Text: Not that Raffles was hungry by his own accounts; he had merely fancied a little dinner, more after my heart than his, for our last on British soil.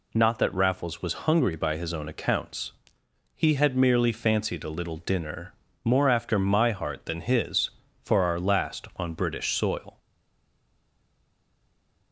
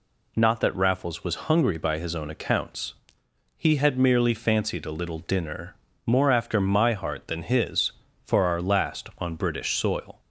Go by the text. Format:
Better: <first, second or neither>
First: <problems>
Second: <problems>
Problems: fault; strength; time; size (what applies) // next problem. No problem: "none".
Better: second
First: stays silent after the last word; from 9.9 s on; 2.2 s long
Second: none